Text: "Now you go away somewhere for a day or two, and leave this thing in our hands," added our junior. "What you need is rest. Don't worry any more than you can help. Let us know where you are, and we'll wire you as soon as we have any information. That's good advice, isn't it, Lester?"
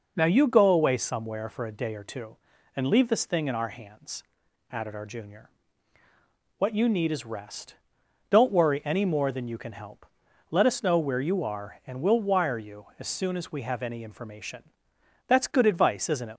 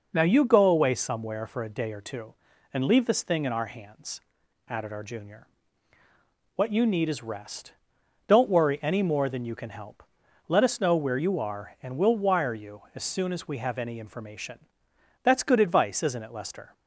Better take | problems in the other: second | stops before "Lester"; at 16.3 s

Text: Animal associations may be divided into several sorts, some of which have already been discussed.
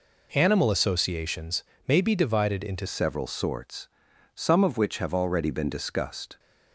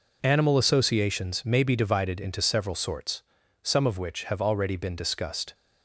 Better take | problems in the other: second | pauses between "associations" and "may"; slight; at 1.6 s; 0.24 s long // changes voice at "several"; from 2.8 s on; 3.5 s long

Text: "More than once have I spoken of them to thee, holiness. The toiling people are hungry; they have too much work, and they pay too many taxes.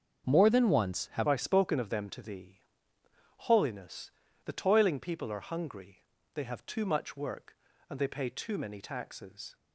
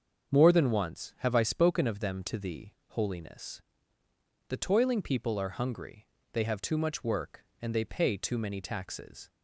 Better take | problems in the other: second | starts louder than the rest; until 1.3 s; 7 dB; also in the second // changes voice at "I"; from 1.2 s on; 8.3 s long

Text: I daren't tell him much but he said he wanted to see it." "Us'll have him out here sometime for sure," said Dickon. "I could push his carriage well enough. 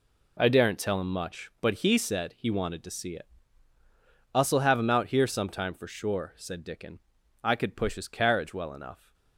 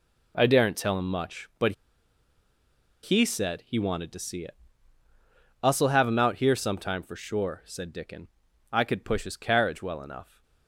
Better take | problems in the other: first | pauses between "but" and "he"; strong; at 1.7 s; 1.3 s long

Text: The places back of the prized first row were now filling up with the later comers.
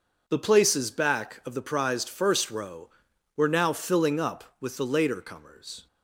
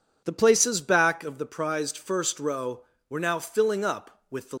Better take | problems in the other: first | stops before "later comers"; at 4.5 s

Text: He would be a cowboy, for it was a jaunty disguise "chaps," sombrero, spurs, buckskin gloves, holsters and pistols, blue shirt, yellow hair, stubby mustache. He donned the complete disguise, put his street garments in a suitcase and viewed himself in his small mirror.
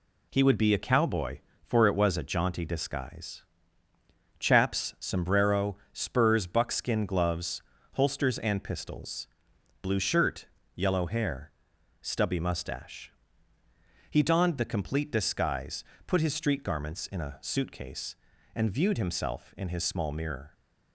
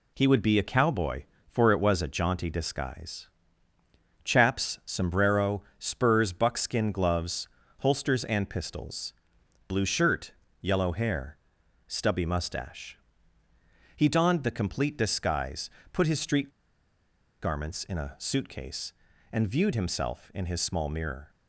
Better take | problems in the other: first | pauses between "disguise" and "chaps"; noticeable; at 3.2 s; 0.96 s long; noticeable in the first // pauses between "street" and "garments"; noticeable; at 16.4 s; 0.93 s long

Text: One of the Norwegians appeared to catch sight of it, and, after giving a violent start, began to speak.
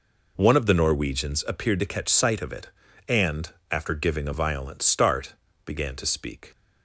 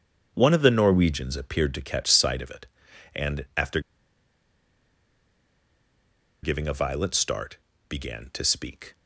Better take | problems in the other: first | starts louder than the rest; strong; until 1.3 s; 7 dB // pauses between "after" and "giving"; strong; at 3.8 s; 2.6 s long

